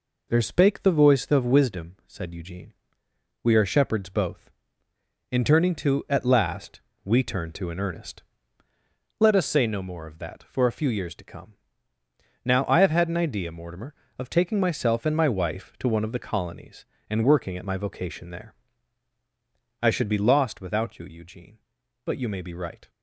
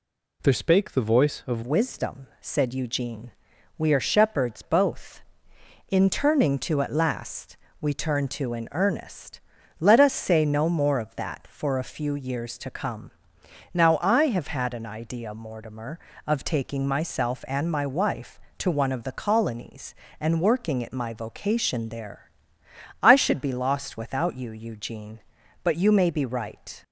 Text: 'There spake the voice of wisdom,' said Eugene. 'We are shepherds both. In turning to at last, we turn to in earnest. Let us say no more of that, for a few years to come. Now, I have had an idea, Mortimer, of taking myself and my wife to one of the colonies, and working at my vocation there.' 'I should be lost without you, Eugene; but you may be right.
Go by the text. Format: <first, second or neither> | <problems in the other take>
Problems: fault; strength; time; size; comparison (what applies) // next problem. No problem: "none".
first | changes voice at "wisdom"; from 1.6 s on; 25.2 s long